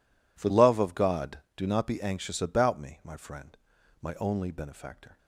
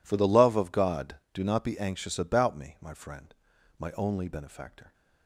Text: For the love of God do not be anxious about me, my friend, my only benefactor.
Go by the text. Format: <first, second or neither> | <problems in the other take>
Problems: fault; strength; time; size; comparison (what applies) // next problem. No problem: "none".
second | skips "the"; at 0.4 s